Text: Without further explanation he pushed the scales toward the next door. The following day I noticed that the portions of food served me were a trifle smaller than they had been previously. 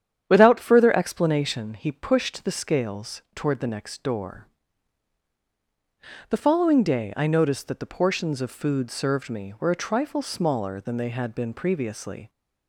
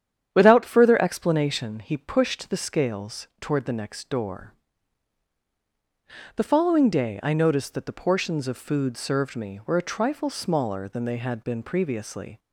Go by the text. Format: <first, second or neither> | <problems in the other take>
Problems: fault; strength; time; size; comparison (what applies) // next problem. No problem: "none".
neither | starts louder than the rest; strong; the same in both